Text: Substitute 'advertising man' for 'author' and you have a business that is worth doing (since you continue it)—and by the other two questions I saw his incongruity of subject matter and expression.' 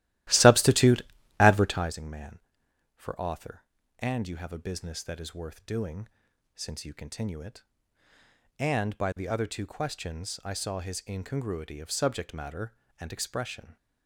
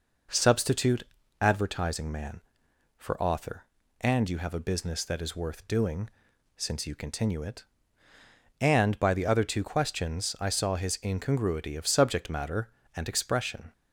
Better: second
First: starts louder than the rest; strong; until 2.0 s; 15.5 dB // pauses between "Substitute" and "advertising"; at 1.0 s; 0.40 s long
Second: pauses between "Substitute" and "advertising"; at 1.0 s; 0.40 s long

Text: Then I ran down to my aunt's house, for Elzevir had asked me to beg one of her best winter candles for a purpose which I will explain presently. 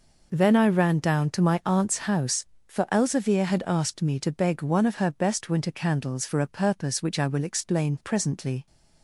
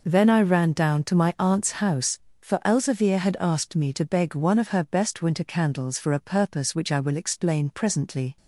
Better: neither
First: none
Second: none

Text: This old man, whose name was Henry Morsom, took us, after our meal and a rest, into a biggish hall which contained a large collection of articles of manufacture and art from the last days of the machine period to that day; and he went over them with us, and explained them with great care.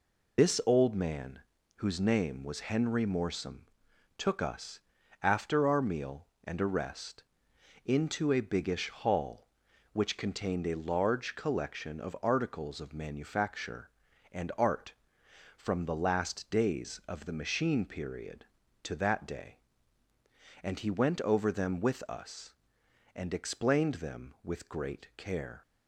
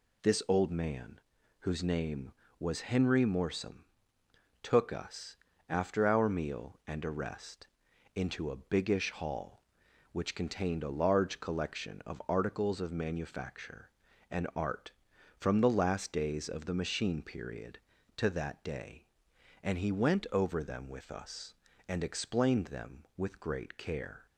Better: second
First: loses the start of "This"; at 0.3 s; 105 ms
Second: none

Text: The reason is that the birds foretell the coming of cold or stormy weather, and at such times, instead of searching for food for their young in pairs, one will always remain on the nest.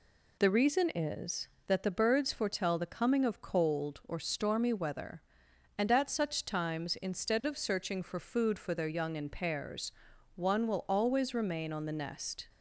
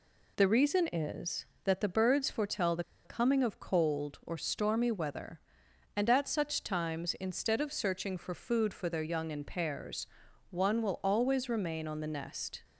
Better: first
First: none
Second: pauses between "the" and "coming"; slight; at 2.8 s; 0.22 s long

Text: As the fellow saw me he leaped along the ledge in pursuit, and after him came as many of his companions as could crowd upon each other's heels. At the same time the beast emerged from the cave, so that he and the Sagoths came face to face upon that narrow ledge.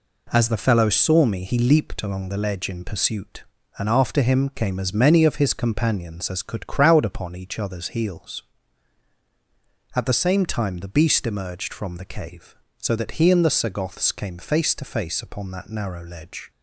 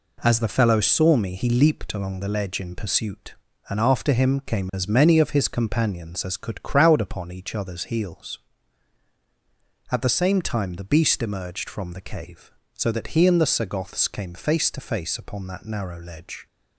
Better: neither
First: none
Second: none

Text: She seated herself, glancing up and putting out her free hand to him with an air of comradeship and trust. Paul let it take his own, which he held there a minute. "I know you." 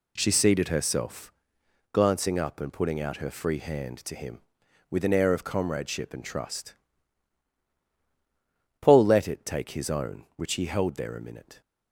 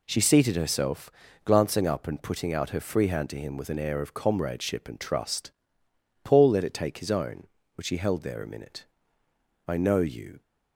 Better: second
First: stops before "I know you"; at 11.6 s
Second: none

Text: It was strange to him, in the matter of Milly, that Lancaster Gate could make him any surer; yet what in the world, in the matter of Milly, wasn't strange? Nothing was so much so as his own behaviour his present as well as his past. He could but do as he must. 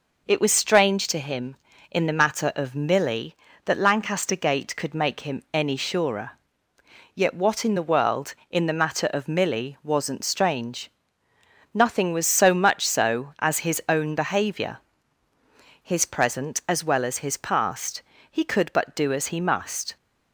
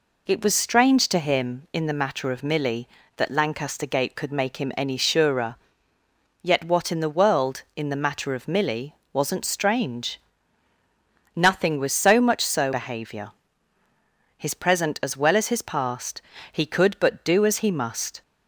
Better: first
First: pauses between "behaviour" and "his"; at 14.7 s; 1.0 s long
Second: skips "as his own"; at 12.7 s // pauses between "behaviour" and "his"; at 13.3 s; 1.0 s long

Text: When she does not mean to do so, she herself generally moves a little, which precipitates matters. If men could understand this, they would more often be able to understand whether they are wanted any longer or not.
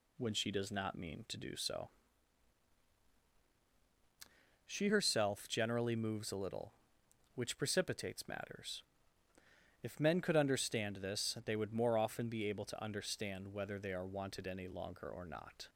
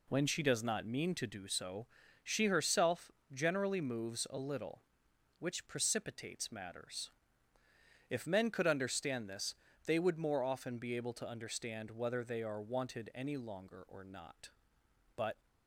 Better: first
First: none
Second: pauses between "herself" and "generally"; slight; at 3.1 s; 0.20 s long // goes on to say "But"; slight; from 15.1 s on; 0.32 s long

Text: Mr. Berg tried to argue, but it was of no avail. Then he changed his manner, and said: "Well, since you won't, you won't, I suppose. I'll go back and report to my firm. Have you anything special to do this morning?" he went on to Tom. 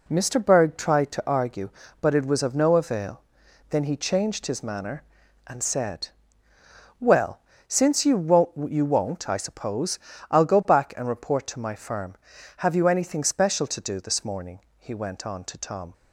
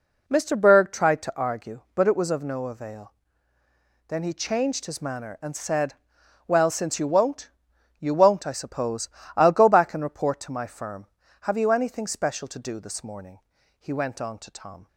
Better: neither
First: none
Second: none

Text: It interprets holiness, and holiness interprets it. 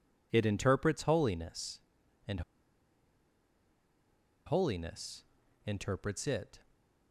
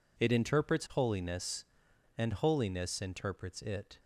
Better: second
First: pauses between "and" and "holiness"; strong; at 2.4 s; 2.0 s long // pauses between "holiness" and "interprets"; at 5.2 s; 0.42 s long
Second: none

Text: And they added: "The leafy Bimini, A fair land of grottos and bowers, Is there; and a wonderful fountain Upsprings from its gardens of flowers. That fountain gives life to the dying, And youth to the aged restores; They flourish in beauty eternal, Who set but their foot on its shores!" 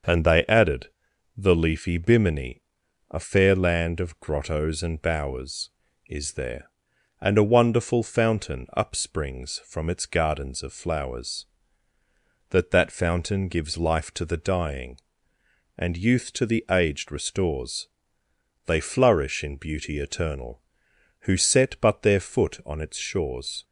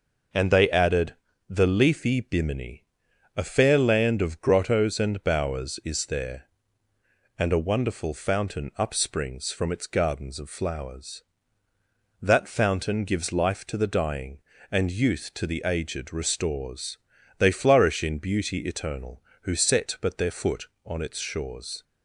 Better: second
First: starts louder than the rest; until 1.5 s; 6.5 dB // says "That" twice; at 12.7 s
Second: none

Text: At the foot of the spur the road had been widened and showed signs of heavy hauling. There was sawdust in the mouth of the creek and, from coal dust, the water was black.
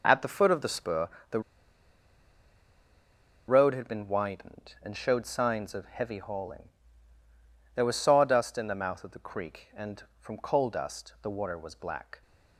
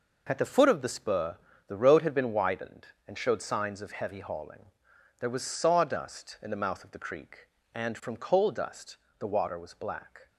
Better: second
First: pauses between "spur" and "the"; slight; at 1.0 s; 0.24 s long // pauses between "the" and "road"; strong; at 1.3 s; 2.0 s long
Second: pauses between "spur" and "the"; slight; at 1.3 s; 0.30 s long

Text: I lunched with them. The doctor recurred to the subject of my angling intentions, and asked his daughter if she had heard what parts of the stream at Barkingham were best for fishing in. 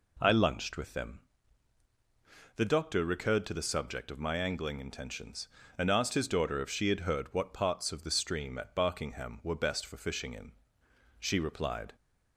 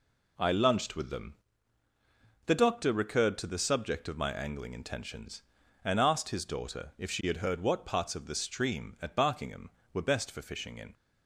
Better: second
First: goes on to say "She replied"; noticeable; from 11.2 s on; 0.72 s long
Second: none

